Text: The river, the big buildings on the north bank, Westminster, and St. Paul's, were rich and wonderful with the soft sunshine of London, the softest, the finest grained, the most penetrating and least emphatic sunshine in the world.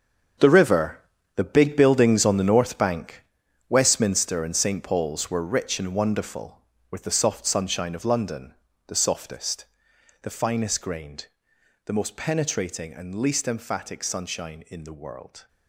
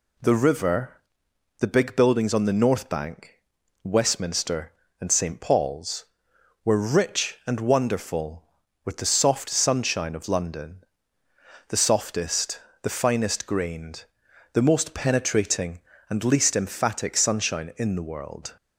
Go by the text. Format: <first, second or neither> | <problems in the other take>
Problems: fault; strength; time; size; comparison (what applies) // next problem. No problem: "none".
second | gets quieter; strong; throughout; 12 dB